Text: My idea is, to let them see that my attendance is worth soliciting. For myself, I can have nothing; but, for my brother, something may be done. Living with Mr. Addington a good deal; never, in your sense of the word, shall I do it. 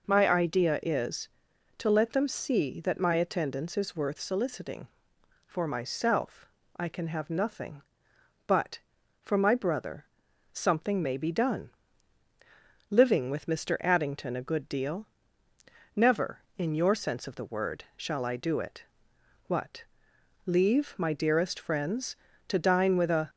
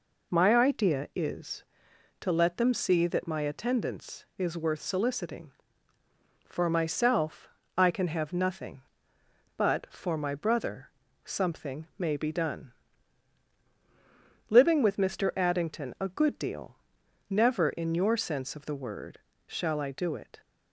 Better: second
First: goes on to say "What leave my dearest friends to dine with a"; strong; from 19.4 s on; 3.8 s long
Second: none

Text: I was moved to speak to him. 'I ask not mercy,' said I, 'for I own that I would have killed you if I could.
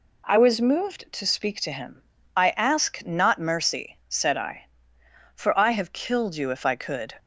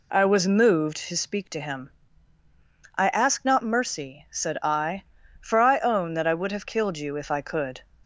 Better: second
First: skips "own that I would"; at 5.7 s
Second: none

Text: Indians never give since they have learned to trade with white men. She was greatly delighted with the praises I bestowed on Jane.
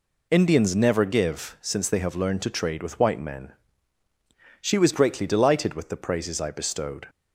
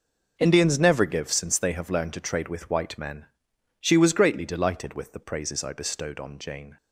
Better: second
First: stops before "on Jane"; at 7.0 s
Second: none

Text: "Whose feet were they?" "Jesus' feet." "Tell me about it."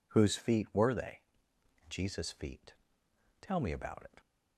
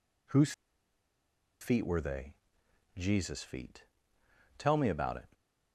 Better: first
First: none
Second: pauses between "Whose" and "feet"; at 0.5 s; 1.0 s long

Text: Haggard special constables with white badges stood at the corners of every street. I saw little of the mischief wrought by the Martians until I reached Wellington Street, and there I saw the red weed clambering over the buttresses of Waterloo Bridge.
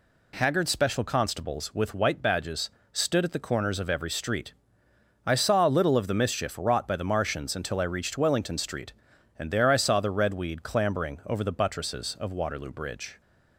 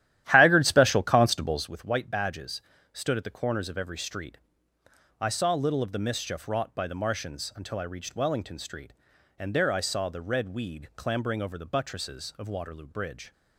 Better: first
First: pauses between "badges" and "stood"; slight; at 2.6 s; 0.24 s long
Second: starts louder than the rest; strong; until 1.8 s; 12.5 dB // pauses between "badges" and "stood"; slight; at 2.6 s; 0.30 s long

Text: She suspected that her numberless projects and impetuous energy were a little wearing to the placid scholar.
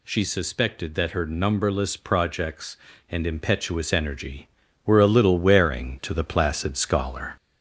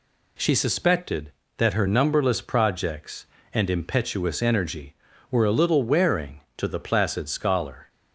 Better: second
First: gets louder; slight; throughout; 3 dB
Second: none

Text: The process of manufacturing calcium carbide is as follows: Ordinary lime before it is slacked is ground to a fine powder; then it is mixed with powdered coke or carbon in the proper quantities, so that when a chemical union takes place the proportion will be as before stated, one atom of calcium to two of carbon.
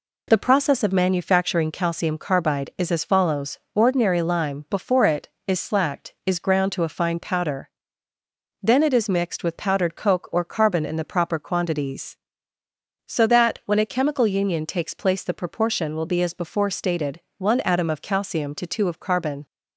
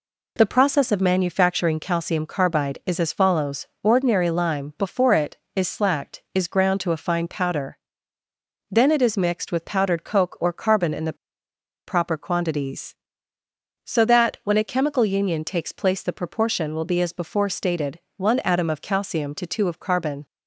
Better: first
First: none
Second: pauses between "the" and "proper"; noticeable; at 11.1 s; 0.72 s long

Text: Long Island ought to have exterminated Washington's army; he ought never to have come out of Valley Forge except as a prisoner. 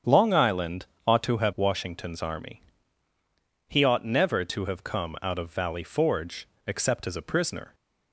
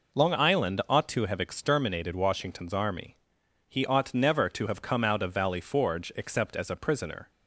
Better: second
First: starts louder than the rest; strong; until 1.2 s; 8 dB // pauses between "Island" and "ought"; slight; at 0.8 s; 0.22 s long // skips "exterminated"; at 1.5 s // pauses between "Forge" and "except"; slight; at 6.4 s; 0.18 s long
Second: none

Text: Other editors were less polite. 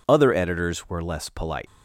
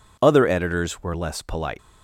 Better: neither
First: none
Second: none

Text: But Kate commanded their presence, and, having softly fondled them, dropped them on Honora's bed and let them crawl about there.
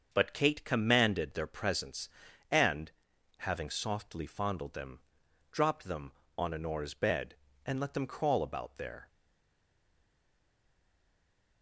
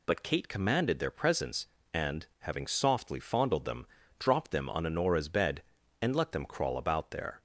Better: second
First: starts louder than the rest; until 1.1 s; 7 dB // stays silent after the last word; strong; from 9.0 s on; 2.6 s long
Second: none

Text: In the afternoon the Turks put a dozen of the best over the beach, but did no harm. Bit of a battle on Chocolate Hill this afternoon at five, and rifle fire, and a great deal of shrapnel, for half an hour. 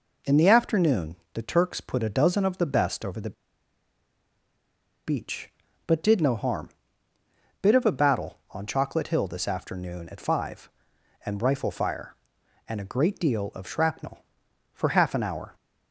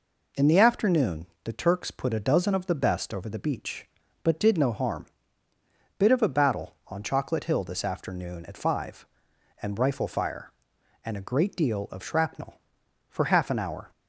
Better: second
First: pauses between "afternoon" and "the"; slight; at 1.1 s; 0.16 s long // pauses between "the" and "beach"; strong; at 3.3 s; 1.7 s long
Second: pauses between "afternoon" and "the"; slight; at 1.2 s; 0.16 s long

